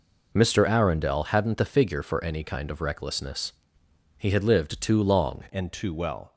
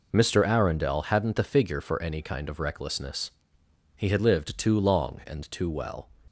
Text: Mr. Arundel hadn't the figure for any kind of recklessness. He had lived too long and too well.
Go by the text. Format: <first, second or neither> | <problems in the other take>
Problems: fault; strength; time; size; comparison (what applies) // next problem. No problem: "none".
second | changes voice at "and"; from 5.5 s on; 0.8 s long